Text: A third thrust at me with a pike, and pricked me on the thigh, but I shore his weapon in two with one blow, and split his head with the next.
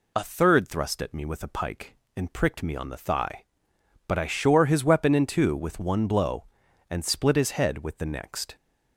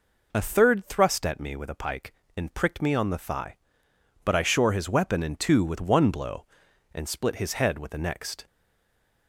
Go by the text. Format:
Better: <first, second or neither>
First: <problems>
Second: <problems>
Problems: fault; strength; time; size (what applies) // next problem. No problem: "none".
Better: first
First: none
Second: stays silent after the last word; slight; from 8.4 s on; 0.8 s long